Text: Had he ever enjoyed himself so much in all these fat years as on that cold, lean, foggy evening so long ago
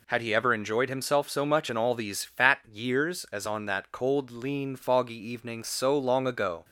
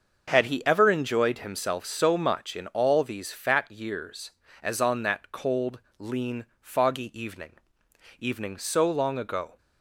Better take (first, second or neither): first